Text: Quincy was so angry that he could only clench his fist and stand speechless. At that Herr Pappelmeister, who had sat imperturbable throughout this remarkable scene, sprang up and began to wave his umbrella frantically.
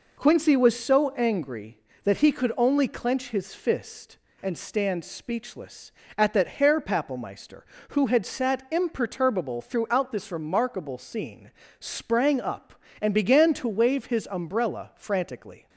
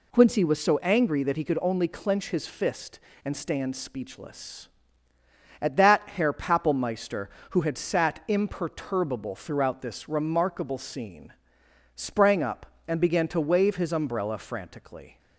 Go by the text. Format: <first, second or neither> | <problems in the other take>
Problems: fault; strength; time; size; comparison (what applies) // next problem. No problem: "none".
neither | none